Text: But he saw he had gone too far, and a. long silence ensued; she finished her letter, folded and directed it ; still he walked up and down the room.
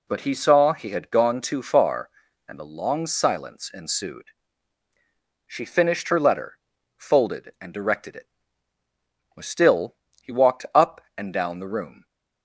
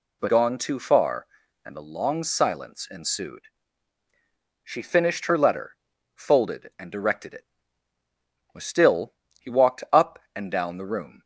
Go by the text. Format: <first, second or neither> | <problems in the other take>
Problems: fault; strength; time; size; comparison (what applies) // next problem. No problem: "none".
first | skips "he saw he had"; at 0.2 s // pauses between "still" and "he"; slight; at 9.1 s; 0.26 s long; slight in the first